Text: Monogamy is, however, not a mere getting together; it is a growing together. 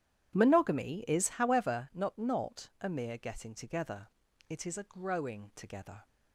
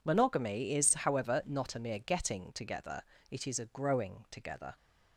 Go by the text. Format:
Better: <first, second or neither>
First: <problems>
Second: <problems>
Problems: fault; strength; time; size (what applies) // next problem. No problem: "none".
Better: second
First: starts louder than the rest; strong; until 1.3 s; 11 dB // says "not" twice; at 2.1 s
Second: none